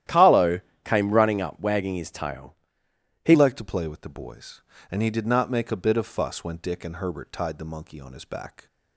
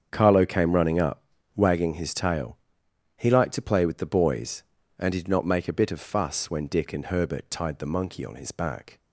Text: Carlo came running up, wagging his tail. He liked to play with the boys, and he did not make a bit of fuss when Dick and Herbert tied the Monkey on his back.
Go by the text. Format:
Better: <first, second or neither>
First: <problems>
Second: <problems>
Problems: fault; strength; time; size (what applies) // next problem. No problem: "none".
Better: second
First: starts louder than the rest; strong; until 1.3 s; 12 dB // pauses between "Carlo" and "came"; slight; at 0.6 s; 0.24 s long // changes voice at "liked"; from 3.3 s on; 5.3 s long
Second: starts louder than the rest; strong; until 1.1 s; 7.5 dB